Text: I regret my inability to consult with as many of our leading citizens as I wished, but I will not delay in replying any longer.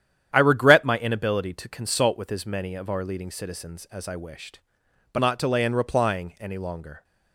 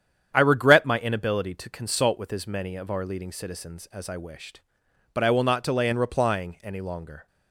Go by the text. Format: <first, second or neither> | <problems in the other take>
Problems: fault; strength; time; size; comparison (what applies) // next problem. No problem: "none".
second | starts louder than the rest; strong; until 1.3 s; 10 dB; strong in the second // skips "I will"; at 5.1 s